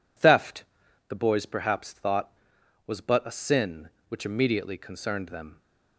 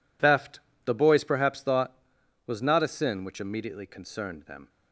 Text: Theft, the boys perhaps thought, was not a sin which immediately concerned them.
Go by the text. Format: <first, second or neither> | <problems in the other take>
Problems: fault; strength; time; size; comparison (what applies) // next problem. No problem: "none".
second | says "but" for "not"; at 3.0 s